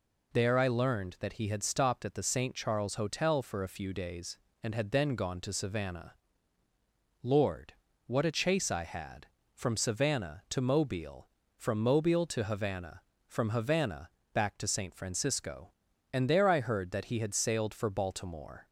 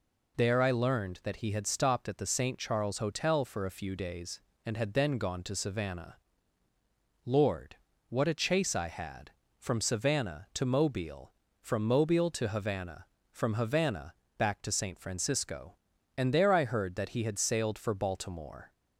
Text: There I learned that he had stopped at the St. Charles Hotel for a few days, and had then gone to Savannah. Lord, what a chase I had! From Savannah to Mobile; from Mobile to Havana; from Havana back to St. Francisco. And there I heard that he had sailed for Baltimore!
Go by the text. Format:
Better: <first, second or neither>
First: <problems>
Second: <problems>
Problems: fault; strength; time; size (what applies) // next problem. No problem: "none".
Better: neither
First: pauses between "Havana" and "back"; slight; at 14.0 s; 0.24 s long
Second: pauses between "Havana" and "back"; slight; at 14.1 s; 0.24 s long